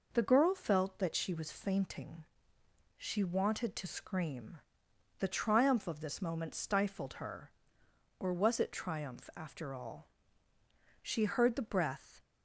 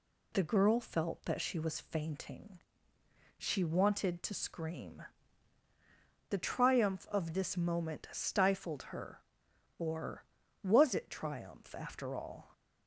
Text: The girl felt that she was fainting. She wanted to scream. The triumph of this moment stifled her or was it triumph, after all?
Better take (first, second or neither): second